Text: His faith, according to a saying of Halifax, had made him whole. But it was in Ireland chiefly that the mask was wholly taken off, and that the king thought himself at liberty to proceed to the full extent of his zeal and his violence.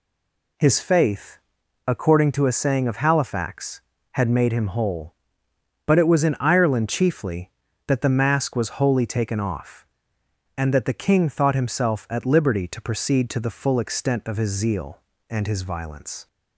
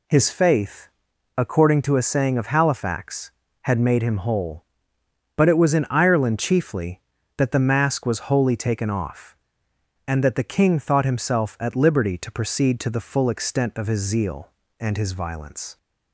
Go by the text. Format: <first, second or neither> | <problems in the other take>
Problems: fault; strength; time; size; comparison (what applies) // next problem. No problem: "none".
second | stays silent before the first word; slight; until 0.5 s; 0.5 s long